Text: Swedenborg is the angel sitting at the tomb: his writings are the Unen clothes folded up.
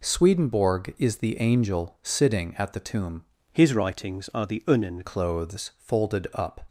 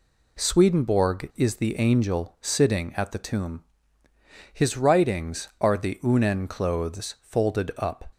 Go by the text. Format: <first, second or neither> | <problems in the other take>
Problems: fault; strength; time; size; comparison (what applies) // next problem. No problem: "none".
second | changes voice from "his" to "Unen"; from 3.5 to 5.0 s; 1.5 s long